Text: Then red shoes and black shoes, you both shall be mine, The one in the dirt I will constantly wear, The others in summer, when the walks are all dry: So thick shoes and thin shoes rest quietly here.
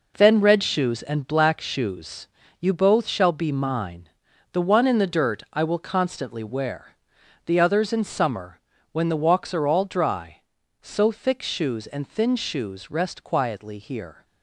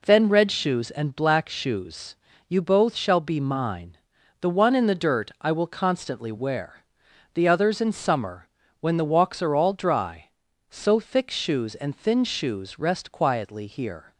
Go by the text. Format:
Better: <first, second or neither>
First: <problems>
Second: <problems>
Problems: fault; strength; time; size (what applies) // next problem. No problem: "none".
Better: second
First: gets quieter; strong; throughout; 8.5 dB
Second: none